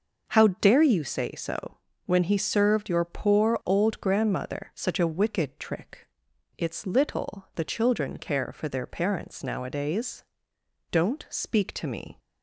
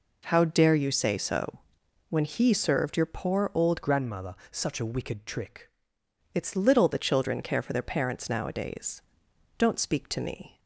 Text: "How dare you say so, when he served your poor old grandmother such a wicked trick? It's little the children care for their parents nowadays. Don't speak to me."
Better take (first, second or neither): first